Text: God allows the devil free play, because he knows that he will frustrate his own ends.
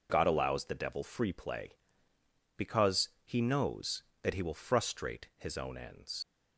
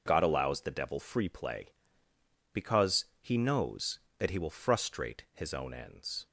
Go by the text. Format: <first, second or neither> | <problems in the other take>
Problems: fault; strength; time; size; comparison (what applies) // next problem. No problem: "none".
second | pauses between "because" and "he"; slight; at 3.0 s; 0.16 s long; slight in the second // leaves "ends" unfinished; at 6.2 s; 80 ms